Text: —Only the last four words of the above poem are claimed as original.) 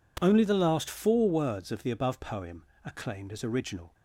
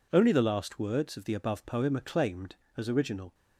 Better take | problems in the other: first | skips "four"; at 0.7 s

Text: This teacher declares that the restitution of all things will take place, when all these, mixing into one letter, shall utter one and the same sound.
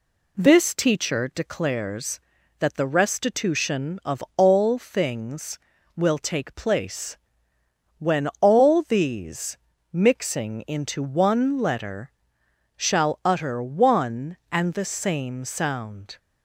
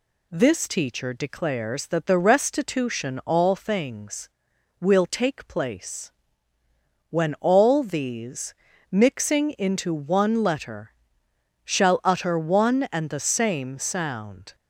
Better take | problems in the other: first | skips "of"; at 3.2 s

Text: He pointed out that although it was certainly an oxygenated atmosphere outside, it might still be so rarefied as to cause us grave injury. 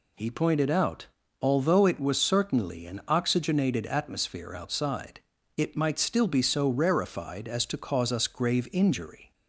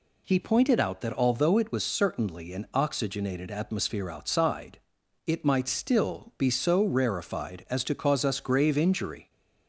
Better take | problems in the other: second | skips "that"; at 1.2 s

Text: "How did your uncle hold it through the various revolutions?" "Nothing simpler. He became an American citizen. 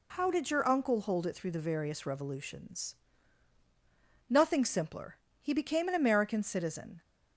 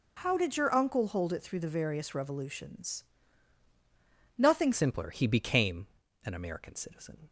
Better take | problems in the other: first | changes voice at "simpler"; from 4.7 s on; 2.5 s long // pauses between "became" and "an"; at 5.8 s; 0.38 s long

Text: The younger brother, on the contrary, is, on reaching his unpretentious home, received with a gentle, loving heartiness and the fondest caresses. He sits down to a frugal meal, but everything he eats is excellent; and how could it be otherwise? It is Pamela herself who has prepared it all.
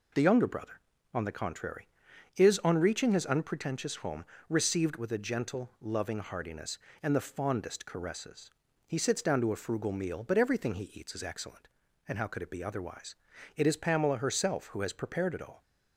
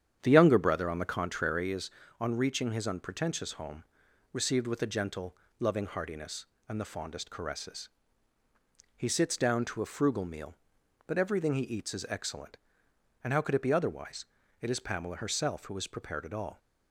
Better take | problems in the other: first | starts louder than the rest; strong; until 1.8 s; 9 dB

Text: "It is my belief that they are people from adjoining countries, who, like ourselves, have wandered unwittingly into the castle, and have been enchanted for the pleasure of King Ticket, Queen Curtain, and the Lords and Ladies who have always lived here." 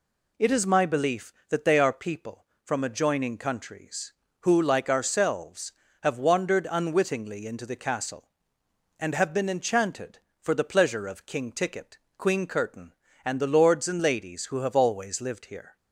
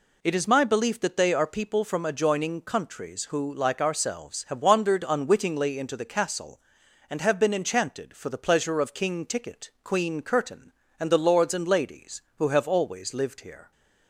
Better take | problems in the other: neither | none

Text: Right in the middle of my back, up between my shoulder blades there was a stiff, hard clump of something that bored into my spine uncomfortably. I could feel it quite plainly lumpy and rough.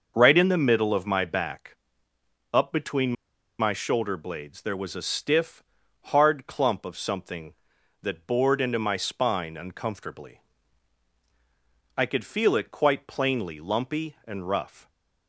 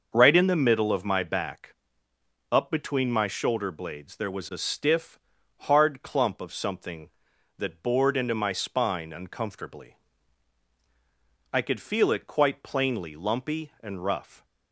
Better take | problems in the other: second | starts louder than the rest; until 1.1 s; 6.5 dB; also in the second // pauses between "between" and "my"; noticeable; at 3.1 s; 0.46 s long

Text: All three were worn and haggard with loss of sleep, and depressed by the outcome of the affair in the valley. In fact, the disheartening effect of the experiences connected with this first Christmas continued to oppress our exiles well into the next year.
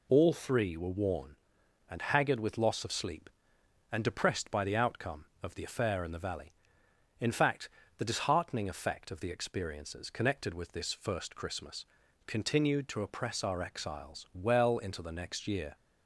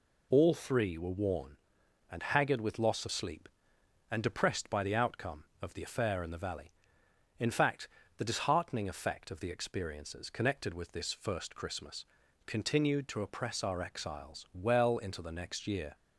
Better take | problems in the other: neither | pauses between "Christmas" and "continued"; the same in both

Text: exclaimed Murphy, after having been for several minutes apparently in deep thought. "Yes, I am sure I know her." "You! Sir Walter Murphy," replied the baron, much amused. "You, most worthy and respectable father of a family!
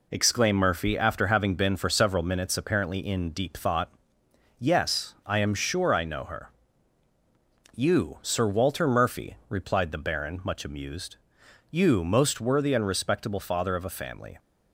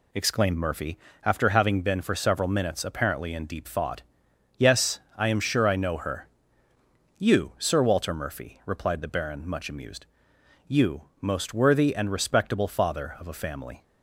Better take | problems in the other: neither | none

